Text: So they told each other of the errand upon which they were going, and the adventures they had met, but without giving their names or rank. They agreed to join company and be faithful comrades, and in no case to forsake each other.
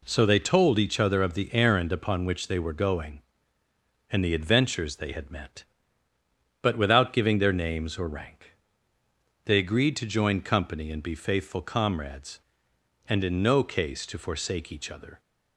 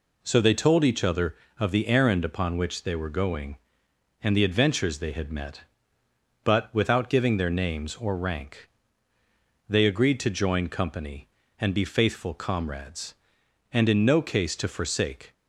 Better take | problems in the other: first | stops before "each other"; at 15.3 s

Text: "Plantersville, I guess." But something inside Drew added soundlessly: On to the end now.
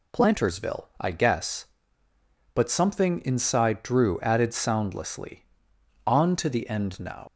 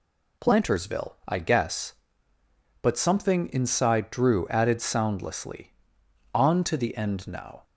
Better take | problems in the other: second | leaves "now" unfinished; at 7.2 s; 85 ms

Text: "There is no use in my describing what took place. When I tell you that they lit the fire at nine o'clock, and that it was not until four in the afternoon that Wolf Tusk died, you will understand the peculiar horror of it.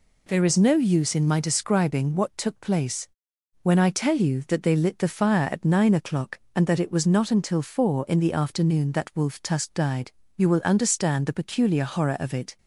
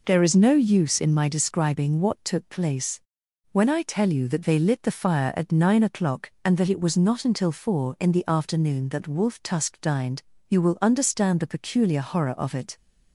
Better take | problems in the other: first | says "dined" for "died"; at 9.7 s

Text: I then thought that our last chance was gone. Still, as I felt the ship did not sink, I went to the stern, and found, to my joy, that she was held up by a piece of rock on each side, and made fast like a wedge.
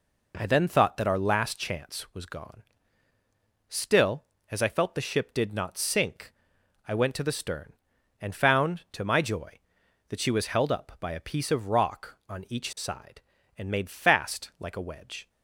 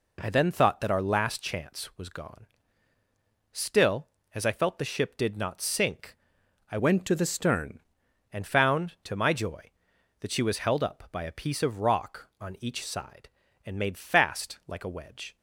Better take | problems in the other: first | changes voice from "went" to "stern"; from 6.7 to 7.7 s; 1.0 s long

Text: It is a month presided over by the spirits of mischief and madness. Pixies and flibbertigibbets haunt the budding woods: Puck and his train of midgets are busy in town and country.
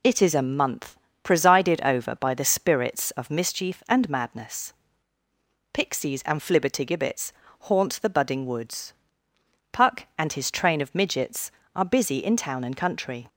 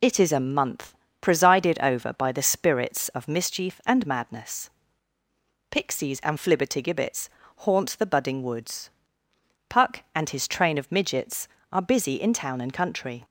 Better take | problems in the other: neither | pauses between "month" and "presided"; slight; the same in both // pauses between "flibbertigibbets" and "haunt"; slight; the same in both

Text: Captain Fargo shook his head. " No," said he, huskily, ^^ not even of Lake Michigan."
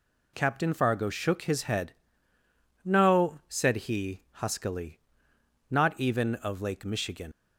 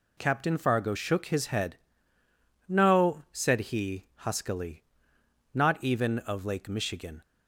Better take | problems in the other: second | leaves "Michigan" unfinished; at 7.3 s; 55 ms

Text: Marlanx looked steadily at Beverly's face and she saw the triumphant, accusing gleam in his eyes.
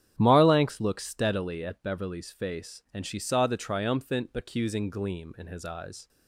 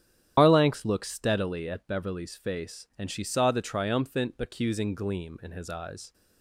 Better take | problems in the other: first | loses the start of "Marlanx"; at 0.3 s; 145 ms // starts louder than the rest; strong; until 1.3 s; 10.5 dB; strong in the first

